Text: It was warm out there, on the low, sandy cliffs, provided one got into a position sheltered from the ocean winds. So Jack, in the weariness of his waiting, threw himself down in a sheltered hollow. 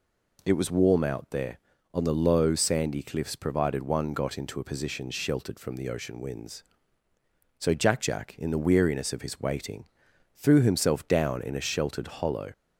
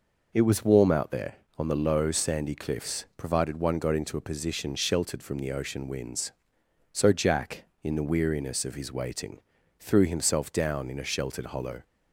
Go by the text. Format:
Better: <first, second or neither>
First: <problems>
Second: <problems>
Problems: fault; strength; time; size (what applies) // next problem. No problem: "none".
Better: second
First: says "Jack" twice; at 8.0 s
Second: none